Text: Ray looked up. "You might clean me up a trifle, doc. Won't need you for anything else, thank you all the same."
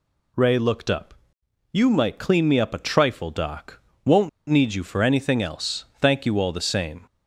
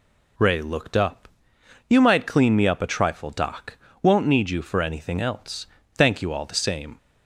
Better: second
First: pauses between "Won't" and "need"; slight; at 4.2 s; 0.20 s long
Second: none

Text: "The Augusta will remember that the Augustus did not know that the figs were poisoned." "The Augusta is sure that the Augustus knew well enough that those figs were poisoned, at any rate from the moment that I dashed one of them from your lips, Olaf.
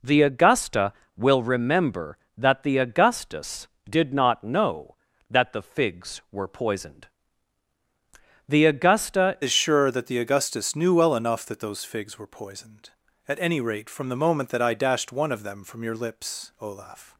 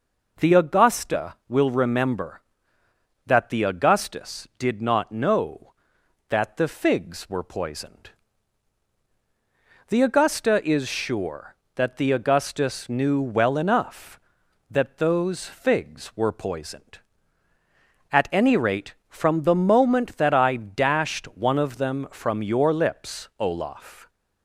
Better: second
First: changes voice at "is"; from 9.4 s on; 7.7 s long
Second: none

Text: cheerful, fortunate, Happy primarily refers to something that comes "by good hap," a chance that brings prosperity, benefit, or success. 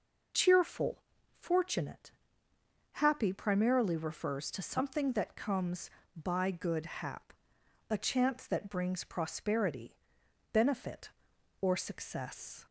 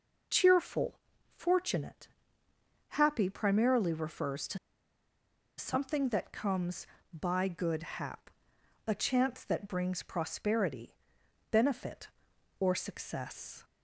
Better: first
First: none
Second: pauses between "to" and "something"; at 4.5 s; 1.0 s long

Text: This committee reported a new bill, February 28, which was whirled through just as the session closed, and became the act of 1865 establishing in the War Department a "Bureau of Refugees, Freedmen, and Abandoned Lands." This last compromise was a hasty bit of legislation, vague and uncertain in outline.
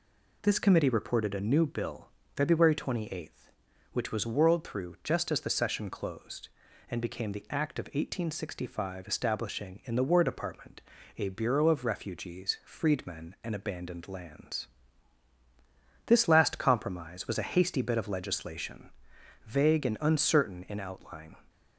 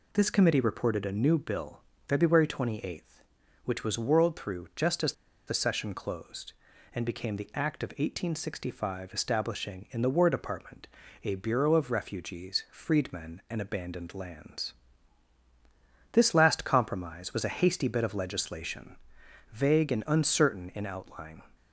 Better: first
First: pauses between "Department" and "a"; slight; at 10.8 s; 0.36 s long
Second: pauses between "as" and "the"; slight; at 5.1 s; 0.34 s long // pauses between "Department" and "a"; slight; at 10.8 s; 0.36 s long

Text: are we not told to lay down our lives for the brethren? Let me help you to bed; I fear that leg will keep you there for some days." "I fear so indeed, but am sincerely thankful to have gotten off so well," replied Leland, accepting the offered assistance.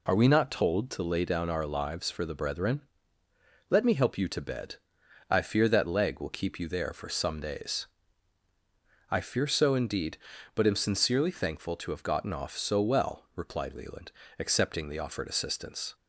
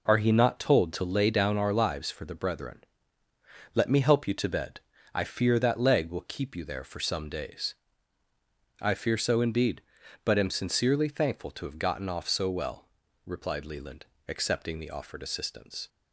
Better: first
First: none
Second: says "he" for "we"; at 0.1 s

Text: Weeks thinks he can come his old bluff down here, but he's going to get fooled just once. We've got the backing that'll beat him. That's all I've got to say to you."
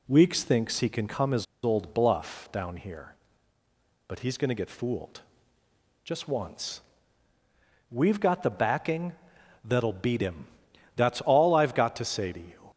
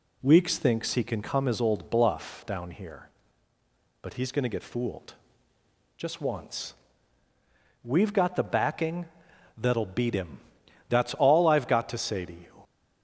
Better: second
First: pauses between "his" and "old"; slight; at 1.4 s; 0.20 s long // pauses between "fooled" and "just"; noticeable; at 5.2 s; 0.84 s long // pauses between "backing" and "that'll"; noticeable; at 9.1 s; 0.54 s long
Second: pauses between "fooled" and "just"; noticeable; at 5.1 s; 0.84 s long // pauses between "backing" and "that'll"; noticeable; at 9.0 s; 0.54 s long

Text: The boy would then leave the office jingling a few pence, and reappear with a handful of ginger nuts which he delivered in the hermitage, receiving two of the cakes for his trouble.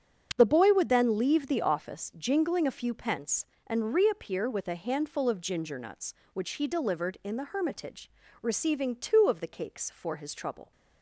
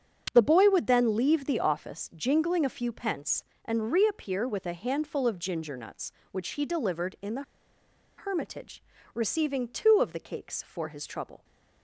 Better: first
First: starts louder than the rest; strong; until 1.3 s; 7.5 dB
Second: starts louder than the rest; strong; until 1.3 s; 7.5 dB // pauses between "the" and "hermitage"; noticeable; at 7.4 s; 0.75 s long

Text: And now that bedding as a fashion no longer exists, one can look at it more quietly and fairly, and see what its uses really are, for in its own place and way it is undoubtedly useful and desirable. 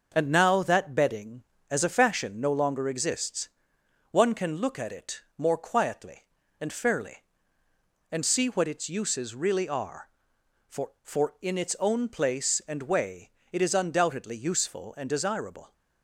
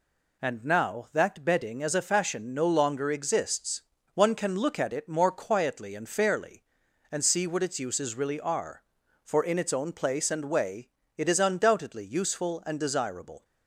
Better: second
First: starts louder than the rest; until 1.1 s; 6.5 dB // pauses between "it" and "more"; slight; at 5.2 s; 0.16 s long // says "for" twice; at 11.0 s // pauses between "way" and "it"; slight; at 13.3 s; 0.20 s long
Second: pauses between "way" and "it"; slight; at 10.8 s; 0.28 s long

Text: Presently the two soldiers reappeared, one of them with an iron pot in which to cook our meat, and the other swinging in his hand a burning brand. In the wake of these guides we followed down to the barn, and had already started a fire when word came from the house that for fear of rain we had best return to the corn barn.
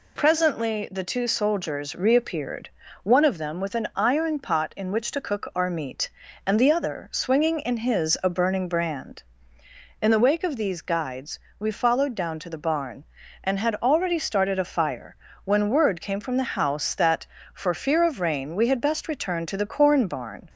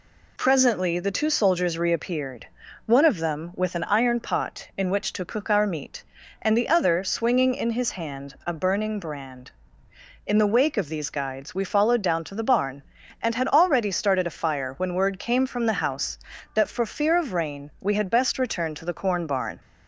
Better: second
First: skips "hand"; at 8.1 s // pauses between "guides" and "we"; slight; at 11.3 s; 0.22 s long // pauses between "fire" and "when"; slight; at 15.1 s; 0.30 s long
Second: none

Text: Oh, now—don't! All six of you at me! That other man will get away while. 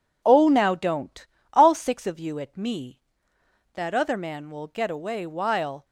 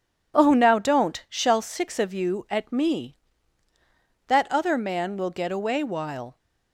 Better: first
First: none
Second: says "Shall" for "All"; at 1.2 s

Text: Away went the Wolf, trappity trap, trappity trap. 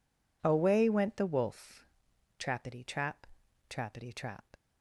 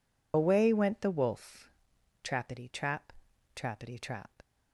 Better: first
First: none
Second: loses the start of "Away"; at 0.3 s; 85 ms

